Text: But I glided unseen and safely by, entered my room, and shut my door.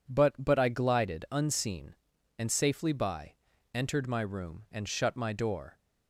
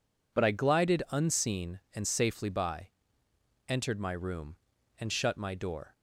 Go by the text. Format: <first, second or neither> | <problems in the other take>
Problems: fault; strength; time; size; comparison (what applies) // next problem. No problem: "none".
second | says "But" twice; at 0.3 s